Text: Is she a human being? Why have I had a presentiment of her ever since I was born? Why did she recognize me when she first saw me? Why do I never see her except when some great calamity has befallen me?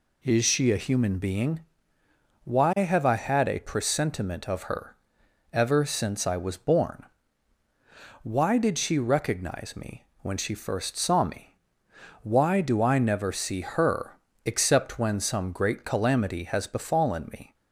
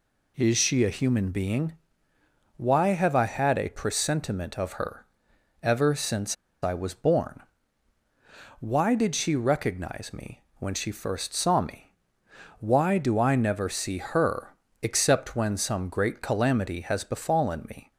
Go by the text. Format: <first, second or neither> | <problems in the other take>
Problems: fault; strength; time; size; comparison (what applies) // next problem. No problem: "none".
first | pauses between "her" and "ever"; noticeable; at 5.0 s; 0.56 s long; noticeable in the first // pauses between "since" and "I"; slight; at 6.3 s; 0.28 s long // pauses between "her" and "except"; slight; at 14.5 s; 0.30 s long; slight in the first